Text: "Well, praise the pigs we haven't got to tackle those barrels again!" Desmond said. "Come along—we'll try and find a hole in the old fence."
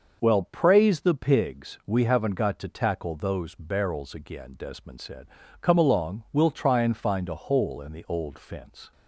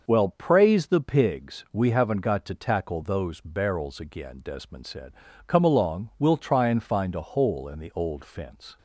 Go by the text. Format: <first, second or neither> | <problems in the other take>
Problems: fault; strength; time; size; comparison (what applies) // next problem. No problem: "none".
neither | starts louder than the rest; noticeable; the same in both